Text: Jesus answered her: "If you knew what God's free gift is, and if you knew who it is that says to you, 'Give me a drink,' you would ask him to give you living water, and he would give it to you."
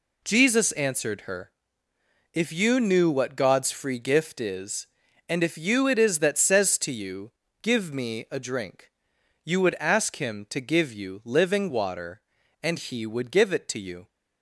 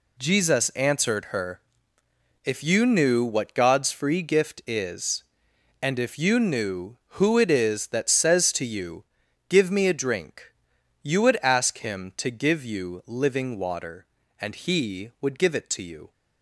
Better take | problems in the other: second | skips "knew who"; at 5.8 s

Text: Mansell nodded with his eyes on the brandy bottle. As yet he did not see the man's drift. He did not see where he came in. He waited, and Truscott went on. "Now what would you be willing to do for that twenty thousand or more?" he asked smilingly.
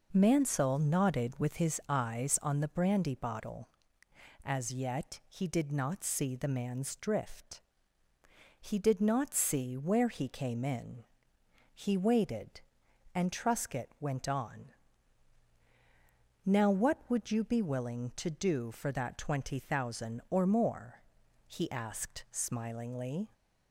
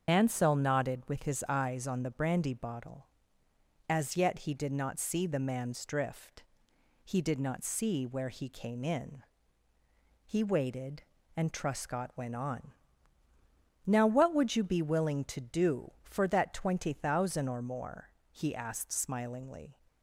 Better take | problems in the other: first | loses the start of "Mansell"; at 0.0 s; 105 ms // starts louder than the rest; strong; until 1.1 s; 7 dB

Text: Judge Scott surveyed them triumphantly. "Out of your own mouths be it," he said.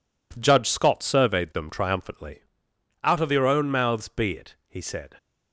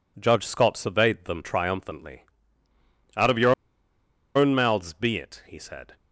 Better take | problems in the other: first | pauses between "your" and "own"; noticeable; at 3.5 s; 0.83 s long

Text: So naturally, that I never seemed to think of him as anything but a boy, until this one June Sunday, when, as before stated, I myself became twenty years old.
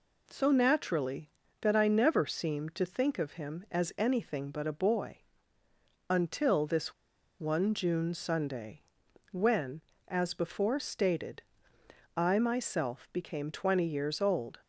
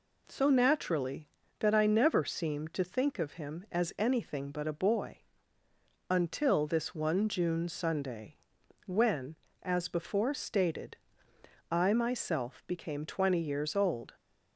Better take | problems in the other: second | pauses between "this" and "one"; noticeable; at 6.9 s; 0.46 s long

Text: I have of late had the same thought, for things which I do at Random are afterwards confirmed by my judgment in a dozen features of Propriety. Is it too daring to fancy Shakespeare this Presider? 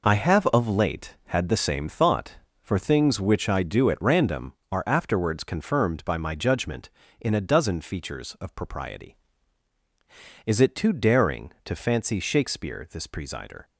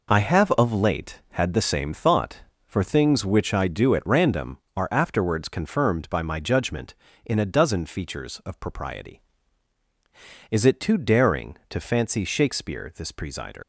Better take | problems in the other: first | leaves "Presider" unfinished; at 13.6 s; 65 ms

